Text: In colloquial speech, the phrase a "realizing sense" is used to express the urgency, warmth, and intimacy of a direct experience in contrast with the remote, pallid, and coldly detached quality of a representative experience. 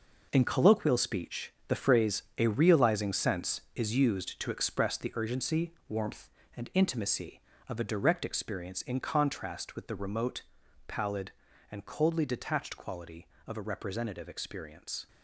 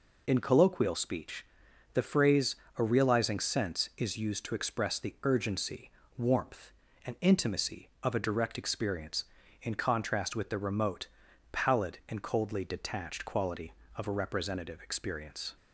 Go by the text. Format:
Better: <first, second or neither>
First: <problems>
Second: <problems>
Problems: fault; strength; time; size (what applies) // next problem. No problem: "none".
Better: second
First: gets quieter; strong; throughout; 10 dB // pauses between "phrase" and "a"; slight; at 2.2 s; 0.16 s long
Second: pauses between "phrase" and "a"; slight; at 2.5 s; 0.22 s long